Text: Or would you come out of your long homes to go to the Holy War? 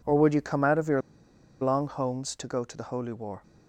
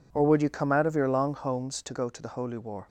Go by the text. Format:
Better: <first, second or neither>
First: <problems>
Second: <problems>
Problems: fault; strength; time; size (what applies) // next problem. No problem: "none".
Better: second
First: pauses between "your" and "long"; noticeable; at 1.0 s; 0.61 s long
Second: none